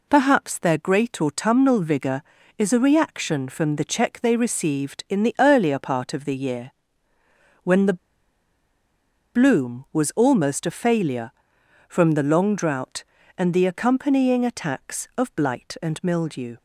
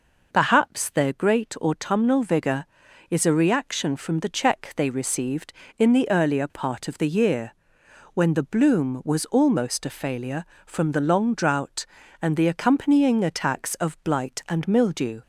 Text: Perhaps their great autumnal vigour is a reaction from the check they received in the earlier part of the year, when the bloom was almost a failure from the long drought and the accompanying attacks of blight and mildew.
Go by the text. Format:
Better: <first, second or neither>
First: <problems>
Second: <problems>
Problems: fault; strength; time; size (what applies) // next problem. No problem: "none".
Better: second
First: pauses between "the" and "bloom"; strong; at 7.9 s; 1.3 s long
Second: none